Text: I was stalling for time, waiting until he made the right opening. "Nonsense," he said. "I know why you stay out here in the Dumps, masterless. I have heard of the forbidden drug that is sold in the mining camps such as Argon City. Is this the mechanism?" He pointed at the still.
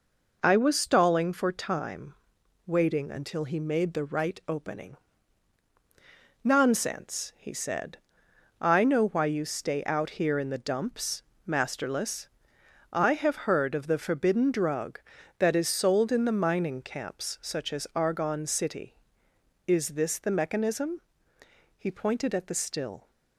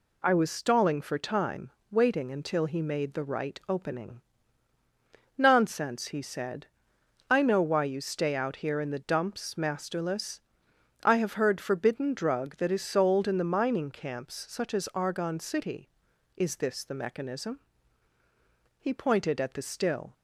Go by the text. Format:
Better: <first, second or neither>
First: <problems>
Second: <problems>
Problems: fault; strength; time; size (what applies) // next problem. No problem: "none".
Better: first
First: none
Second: skips "of the"; at 11.5 s